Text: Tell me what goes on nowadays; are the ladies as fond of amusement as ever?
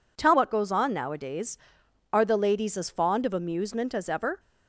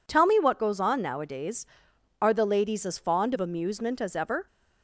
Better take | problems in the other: second | skips "me"; at 0.3 s

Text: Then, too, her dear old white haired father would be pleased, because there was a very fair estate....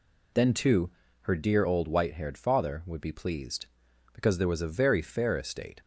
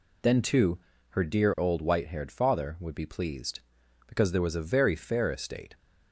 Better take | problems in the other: neither | none

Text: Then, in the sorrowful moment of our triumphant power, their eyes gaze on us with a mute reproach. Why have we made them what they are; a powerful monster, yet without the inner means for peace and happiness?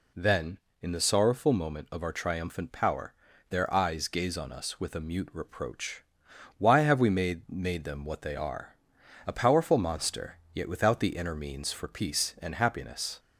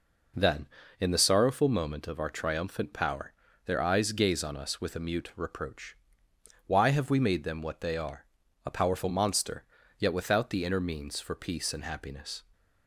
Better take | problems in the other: second | says "made" twice; at 7.4 s

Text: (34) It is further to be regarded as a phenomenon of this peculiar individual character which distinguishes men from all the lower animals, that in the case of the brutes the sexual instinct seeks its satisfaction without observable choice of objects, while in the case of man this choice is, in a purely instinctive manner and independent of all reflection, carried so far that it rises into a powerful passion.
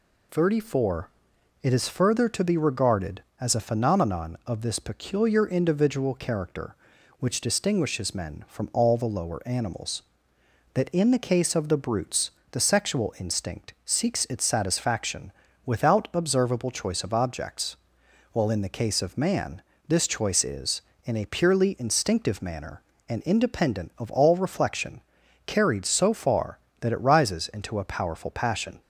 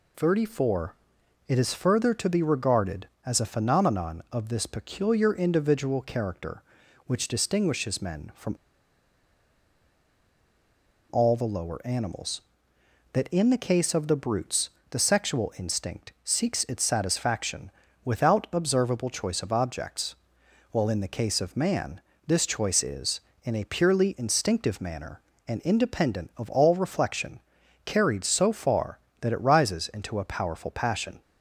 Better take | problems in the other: first | pauses between "from" and "all"; strong; at 8.5 s; 2.5 s long // pauses between "brutes" and "the"; slight; at 14.6 s; 0.22 s long; slight in the first // pauses between "satisfaction" and "without"; slight; at 17.7 s; 0.32 s long; slight in the first // pauses between "man" and "this"; slight; at 22.0 s; 0.26 s long; slight in the first

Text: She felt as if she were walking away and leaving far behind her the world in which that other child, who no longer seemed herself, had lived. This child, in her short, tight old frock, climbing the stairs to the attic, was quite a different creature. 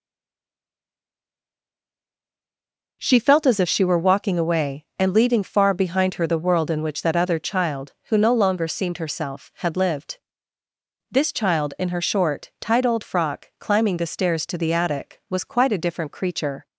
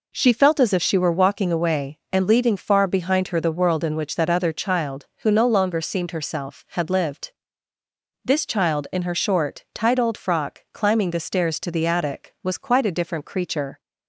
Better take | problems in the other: second | stays silent before the first word; strong; until 3.0 s; 3.0 s long

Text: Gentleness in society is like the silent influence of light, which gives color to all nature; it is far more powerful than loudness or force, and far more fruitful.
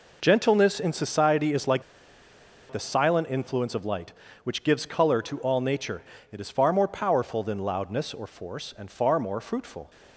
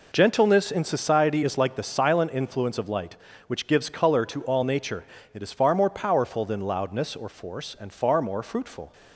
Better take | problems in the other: second | pauses between "like" and "the"; noticeable; at 1.8 s; 0.89 s long

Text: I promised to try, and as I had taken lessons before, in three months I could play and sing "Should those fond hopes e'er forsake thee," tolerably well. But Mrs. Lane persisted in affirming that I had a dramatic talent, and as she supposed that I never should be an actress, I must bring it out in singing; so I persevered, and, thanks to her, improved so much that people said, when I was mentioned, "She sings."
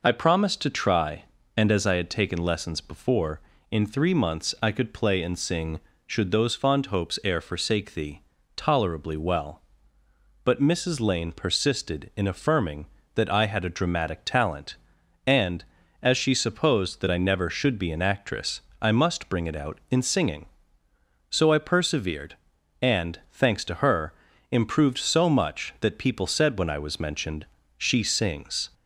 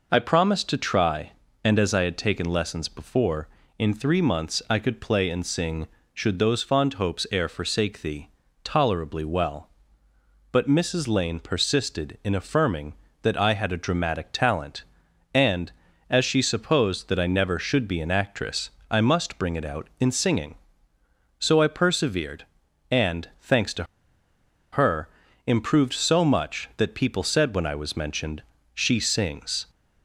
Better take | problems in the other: first | pauses between "to" and "her"; noticeable; at 23.8 s; 0.88 s long

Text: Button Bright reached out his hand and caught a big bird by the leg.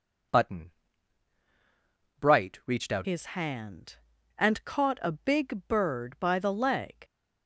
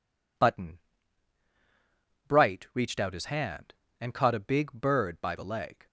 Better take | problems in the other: second | pauses between "Button" and "Bright"; strong; at 0.7 s; 1.4 s long; strong in the second // changes voice at "his"; from 3.0 s on; 4.0 s long

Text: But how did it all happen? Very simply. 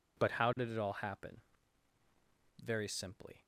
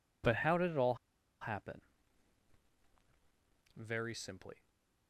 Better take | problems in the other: first | pauses between "all" and "happen"; noticeable; at 0.9 s; 0.46 s long // stays silent after the last word; slight; from 4.5 s on; 0.5 s long

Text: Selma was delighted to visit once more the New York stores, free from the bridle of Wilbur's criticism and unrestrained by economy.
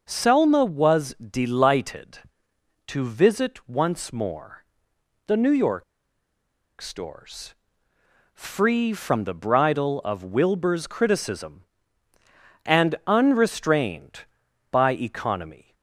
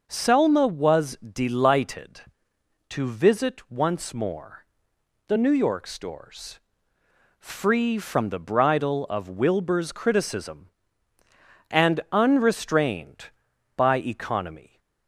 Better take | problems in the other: second | pauses between "more" and "the"; noticeable; at 4.6 s; 0.62 s long; noticeable in the second // pauses between "York" and "stores"; noticeable; at 5.8 s; 0.97 s long

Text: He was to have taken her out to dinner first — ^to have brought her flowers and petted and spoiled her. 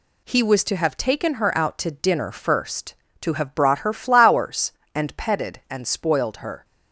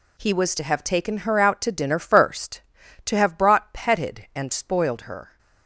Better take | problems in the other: first | skips "her flowers and"; at 3.7 s

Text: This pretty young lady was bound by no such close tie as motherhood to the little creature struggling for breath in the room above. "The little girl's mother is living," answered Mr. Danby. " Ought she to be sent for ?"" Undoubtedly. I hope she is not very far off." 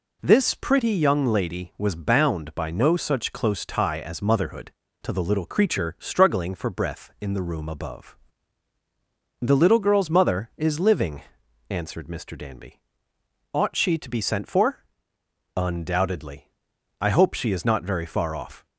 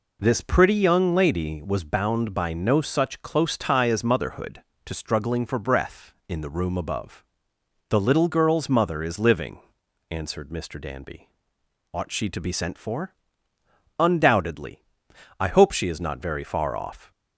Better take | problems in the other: first | skips "the little creature"; at 4.9 s

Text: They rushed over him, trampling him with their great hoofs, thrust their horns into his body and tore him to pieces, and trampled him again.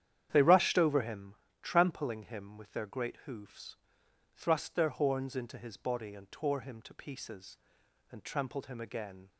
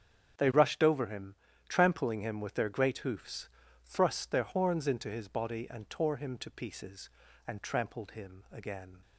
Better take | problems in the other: neither | starts louder than the rest; strong; the same in both

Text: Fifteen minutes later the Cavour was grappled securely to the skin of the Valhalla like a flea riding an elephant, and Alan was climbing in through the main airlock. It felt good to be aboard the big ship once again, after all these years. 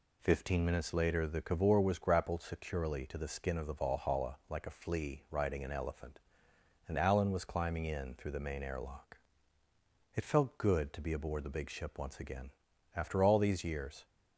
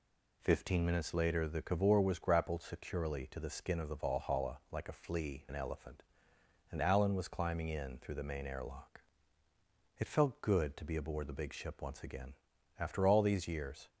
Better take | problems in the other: first | skips "riding"; at 5.4 s

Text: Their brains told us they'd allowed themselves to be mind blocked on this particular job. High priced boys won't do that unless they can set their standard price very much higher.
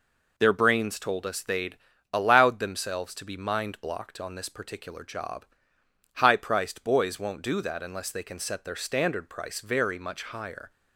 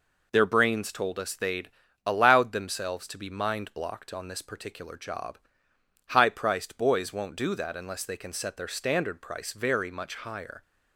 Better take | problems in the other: neither | pauses between "they'd" and "allowed"; slight; the same in both

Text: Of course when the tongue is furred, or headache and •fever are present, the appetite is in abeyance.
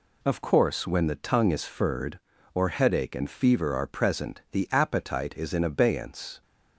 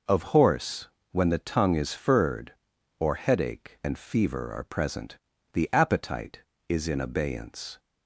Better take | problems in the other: first | says "horse" for "course"; at 0.2 s

